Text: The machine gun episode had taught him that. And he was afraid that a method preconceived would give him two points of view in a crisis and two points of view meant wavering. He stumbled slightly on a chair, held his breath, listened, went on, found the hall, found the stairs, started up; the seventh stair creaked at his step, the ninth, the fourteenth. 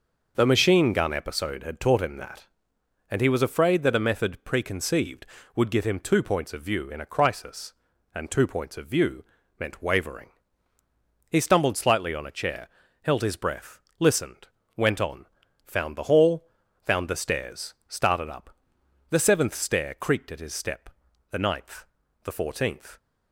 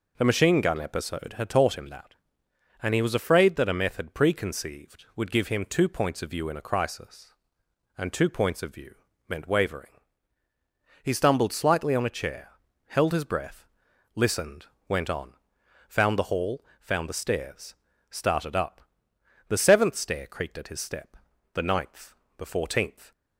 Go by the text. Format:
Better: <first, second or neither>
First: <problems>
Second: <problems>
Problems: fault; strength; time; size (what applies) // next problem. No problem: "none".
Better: neither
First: pauses between "view" and "meant"; slight; at 9.2 s; 0.34 s long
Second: pauses between "view" and "meant"; slight; at 8.9 s; 0.32 s long